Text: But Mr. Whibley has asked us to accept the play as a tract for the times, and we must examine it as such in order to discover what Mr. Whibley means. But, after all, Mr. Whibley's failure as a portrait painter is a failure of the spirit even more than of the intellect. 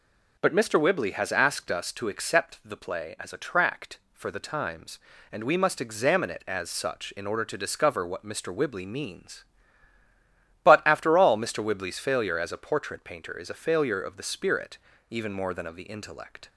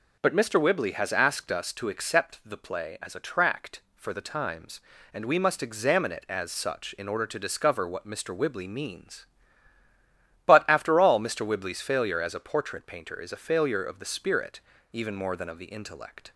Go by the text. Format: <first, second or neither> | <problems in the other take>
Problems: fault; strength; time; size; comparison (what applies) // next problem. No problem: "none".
neither | pauses between "spirit" and "even"; slight; the same in both